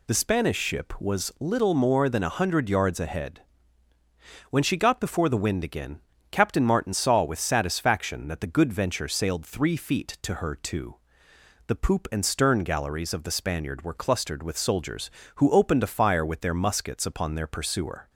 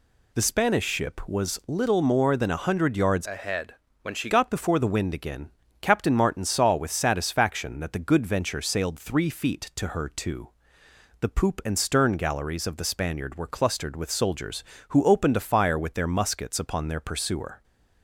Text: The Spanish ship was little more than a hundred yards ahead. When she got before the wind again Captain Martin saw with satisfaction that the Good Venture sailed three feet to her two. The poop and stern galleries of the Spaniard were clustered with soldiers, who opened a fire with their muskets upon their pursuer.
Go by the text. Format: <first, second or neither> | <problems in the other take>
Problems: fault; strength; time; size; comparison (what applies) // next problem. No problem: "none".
first | changes voice from "ahead" to "she"; from 3.2 to 4.2 s; 1.0 s long // pauses between "again" and "Captain"; slight; at 5.4 s; 0.32 s long; slight in the first